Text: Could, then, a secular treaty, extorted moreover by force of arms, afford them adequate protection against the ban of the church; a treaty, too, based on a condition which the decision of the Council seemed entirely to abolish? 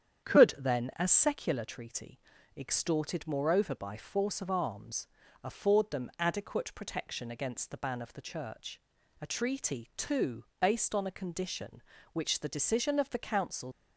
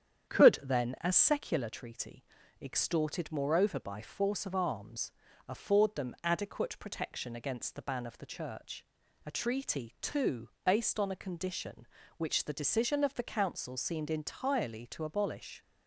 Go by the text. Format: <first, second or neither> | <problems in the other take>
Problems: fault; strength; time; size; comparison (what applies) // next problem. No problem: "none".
second | starts louder than the rest; strong; until 1.3 s; 8.5 dB; strong in the second // stops before "seemed entirely to abolish"; at 13.7 s